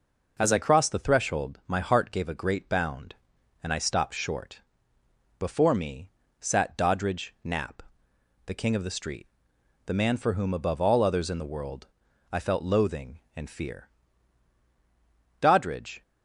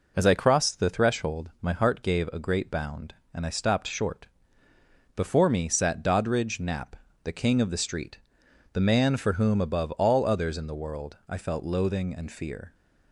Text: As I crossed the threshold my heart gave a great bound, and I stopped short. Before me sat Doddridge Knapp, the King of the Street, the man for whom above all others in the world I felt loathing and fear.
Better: second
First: pauses between "me" and "sat"; slight; at 6.1 s; 0.28 s long // pauses between "world" and "I"; at 11.8 s; 0.44 s long // goes on to say "Doddridge"; noticeable; from 15.3 s on; 0.62 s long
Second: none

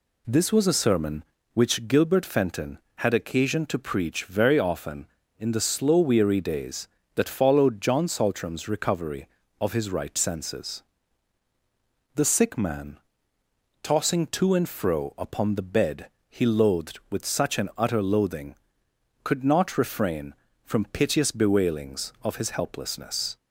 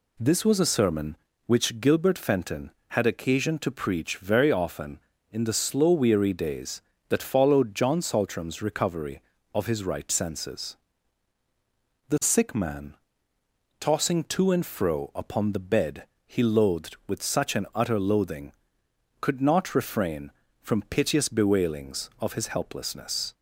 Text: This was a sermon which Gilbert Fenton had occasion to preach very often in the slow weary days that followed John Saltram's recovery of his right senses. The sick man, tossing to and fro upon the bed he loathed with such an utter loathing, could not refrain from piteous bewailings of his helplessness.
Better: neither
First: pauses between "bed" and "he"; slight; at 16.0 s; 0.24 s long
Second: pauses between "bed" and "he"; slight; at 16.0 s; 0.24 s long

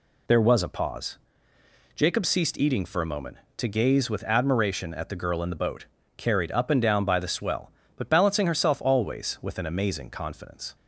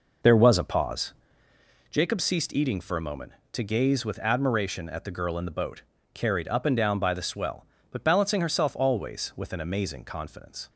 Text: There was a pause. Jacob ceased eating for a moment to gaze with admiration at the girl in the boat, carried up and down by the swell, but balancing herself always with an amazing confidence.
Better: first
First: none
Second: starts louder than the rest; noticeable; until 1.6 s; 5 dB

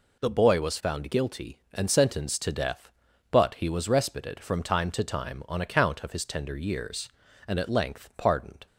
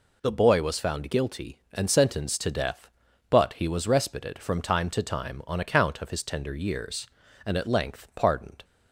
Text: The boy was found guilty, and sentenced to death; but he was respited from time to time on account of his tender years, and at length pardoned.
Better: neither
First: none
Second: none

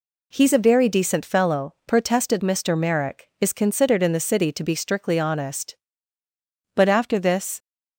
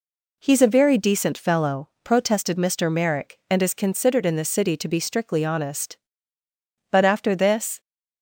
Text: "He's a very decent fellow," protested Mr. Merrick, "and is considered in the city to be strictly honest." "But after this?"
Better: second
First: skips "and"; at 3.3 s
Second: none

